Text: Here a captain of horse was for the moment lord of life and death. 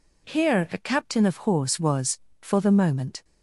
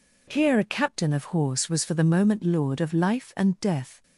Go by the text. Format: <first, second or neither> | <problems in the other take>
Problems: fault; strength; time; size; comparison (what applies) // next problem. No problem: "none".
second | stops before "lord of life and death"; at 3.2 s